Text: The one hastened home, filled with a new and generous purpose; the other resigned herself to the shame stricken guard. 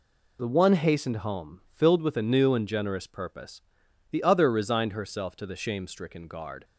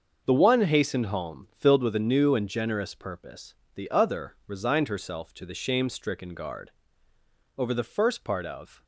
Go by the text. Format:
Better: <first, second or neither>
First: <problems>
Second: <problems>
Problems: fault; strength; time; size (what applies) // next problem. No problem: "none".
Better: first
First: none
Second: starts louder than the rest; until 1.2 s; 6.5 dB // goes on to say "Over the first part of"; noticeable; from 7.5 s on; 1.2 s long